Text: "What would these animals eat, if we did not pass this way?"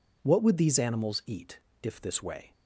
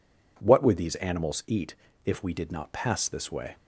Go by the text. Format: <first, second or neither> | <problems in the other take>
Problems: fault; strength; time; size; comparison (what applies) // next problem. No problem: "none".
second | skips "we did not pass"; at 2.0 s